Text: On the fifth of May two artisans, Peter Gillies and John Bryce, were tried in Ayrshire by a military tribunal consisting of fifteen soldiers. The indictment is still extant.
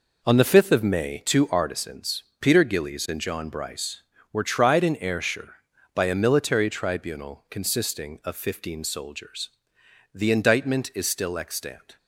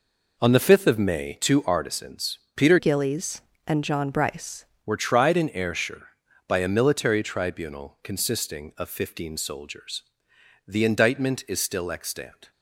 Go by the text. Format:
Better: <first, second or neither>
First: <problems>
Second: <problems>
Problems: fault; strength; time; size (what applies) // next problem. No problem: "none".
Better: first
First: none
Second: changes voice from "Gillies" to "Bryce"; from 2.7 to 4.6 s; 1.9 s long